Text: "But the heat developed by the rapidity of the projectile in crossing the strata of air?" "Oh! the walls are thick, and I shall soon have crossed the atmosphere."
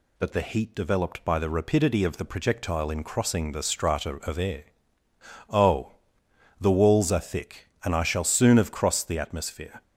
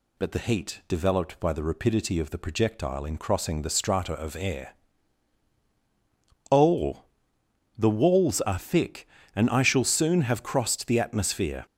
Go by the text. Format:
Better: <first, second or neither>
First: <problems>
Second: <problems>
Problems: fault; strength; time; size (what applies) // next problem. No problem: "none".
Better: neither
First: none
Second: none